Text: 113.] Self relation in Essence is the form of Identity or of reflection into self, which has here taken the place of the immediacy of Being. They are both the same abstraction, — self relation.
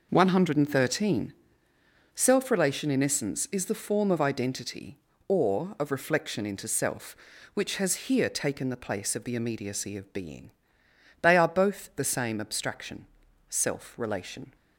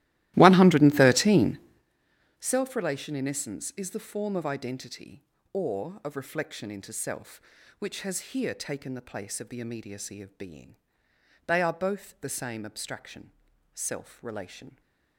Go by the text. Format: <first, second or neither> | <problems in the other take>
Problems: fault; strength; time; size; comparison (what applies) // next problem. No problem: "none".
first | starts louder than the rest; strong; until 1.9 s; 16.5 dB